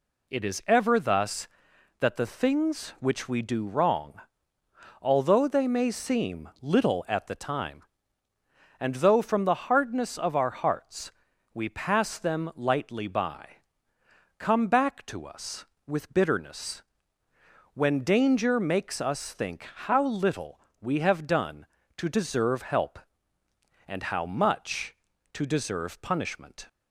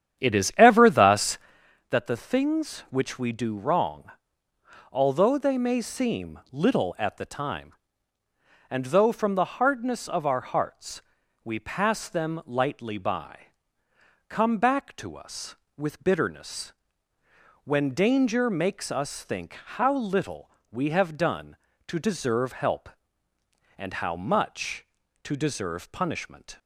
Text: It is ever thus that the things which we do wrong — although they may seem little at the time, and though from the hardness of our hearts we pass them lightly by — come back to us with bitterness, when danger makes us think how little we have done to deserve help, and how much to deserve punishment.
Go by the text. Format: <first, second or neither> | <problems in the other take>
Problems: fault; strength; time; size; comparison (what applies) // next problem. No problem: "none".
first | starts louder than the rest; strong; until 1.7 s; 9.5 dB // pauses between "hearts" and "we"; at 11.0 s; 0.42 s long; also in the first // pauses between "think" and "how"; slight; at 19.5 s; 0.22 s long; slight in the first // pauses between "little" and "we"; slight; at 20.4 s; 0.22 s long; slight in the first